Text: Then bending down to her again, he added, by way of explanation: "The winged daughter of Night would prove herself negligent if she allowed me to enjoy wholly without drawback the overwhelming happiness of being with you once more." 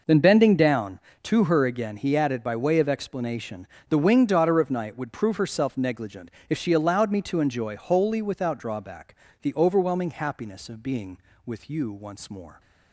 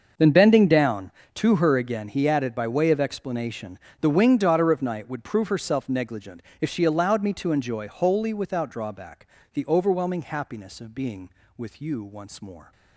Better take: first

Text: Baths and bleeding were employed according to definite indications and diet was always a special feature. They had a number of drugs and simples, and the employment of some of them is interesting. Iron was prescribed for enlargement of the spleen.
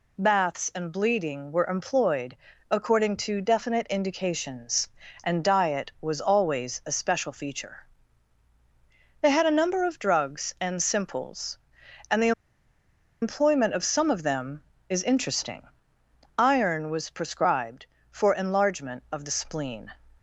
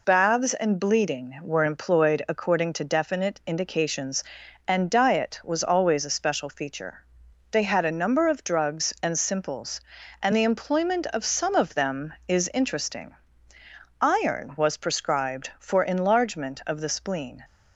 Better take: second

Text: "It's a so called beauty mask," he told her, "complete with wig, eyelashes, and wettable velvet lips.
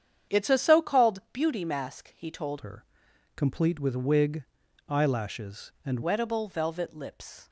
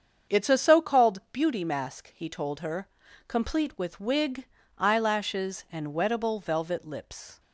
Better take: second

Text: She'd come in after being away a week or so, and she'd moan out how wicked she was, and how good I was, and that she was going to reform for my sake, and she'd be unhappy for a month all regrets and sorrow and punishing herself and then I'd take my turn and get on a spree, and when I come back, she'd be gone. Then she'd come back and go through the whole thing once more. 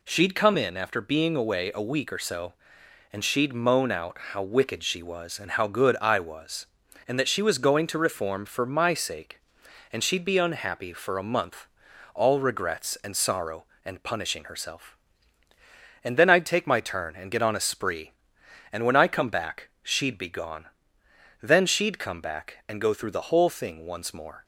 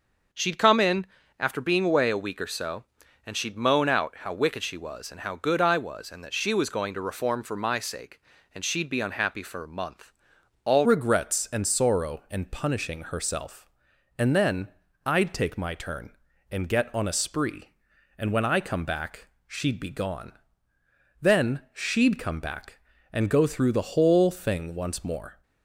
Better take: first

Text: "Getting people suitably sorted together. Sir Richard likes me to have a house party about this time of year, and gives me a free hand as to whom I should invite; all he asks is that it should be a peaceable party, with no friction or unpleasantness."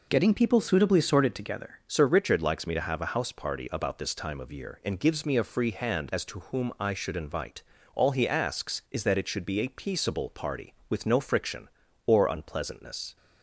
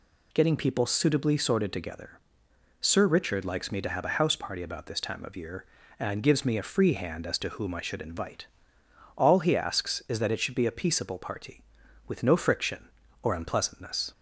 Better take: second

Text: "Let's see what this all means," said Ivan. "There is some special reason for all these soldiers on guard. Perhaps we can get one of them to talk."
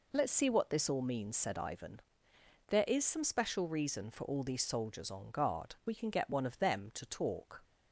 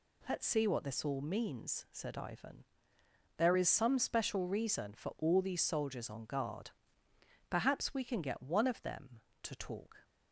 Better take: second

